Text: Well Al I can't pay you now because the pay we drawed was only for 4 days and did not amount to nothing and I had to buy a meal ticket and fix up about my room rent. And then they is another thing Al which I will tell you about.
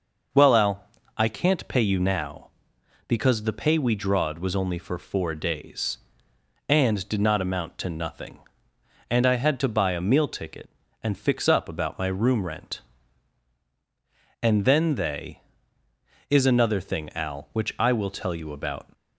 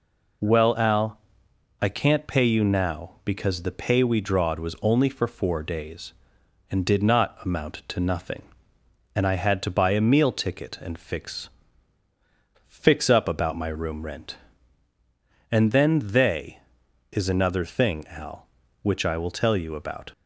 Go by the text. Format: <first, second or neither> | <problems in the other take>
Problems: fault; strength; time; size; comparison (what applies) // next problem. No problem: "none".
first | pauses between "Al" and "I"; noticeable; at 1.1 s; 0.62 s long; slight in the first // says "fix" twice; at 12.6 s